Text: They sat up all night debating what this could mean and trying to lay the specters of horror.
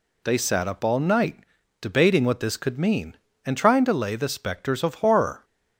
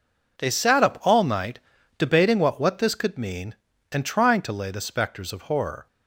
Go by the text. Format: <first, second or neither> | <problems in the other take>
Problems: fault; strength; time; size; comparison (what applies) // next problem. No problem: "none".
first | pauses between "night" and "debating"; at 1.5 s; 0.38 s long; also in the first // says "what" twice; at 2.6 s